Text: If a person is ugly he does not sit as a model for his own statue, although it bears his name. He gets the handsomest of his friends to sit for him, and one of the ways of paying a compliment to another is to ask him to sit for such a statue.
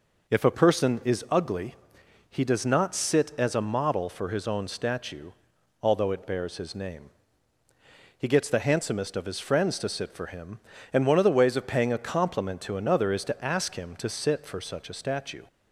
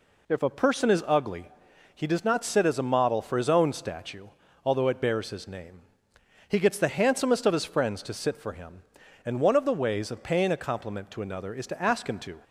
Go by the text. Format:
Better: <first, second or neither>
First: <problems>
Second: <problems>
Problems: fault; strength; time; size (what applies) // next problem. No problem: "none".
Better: first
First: pauses between "ugly" and "he"; noticeable; at 1.7 s; 0.54 s long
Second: pauses between "ugly" and "he"; noticeable; at 1.5 s; 0.46 s long // stops before "sit for such a statue"; at 12.4 s